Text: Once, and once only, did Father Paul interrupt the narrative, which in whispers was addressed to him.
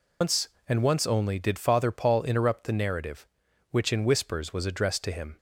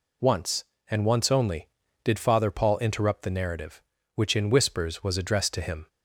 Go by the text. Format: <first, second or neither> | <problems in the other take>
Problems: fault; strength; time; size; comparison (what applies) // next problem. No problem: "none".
second | loses the start of "Once"; at 0.2 s; 140 ms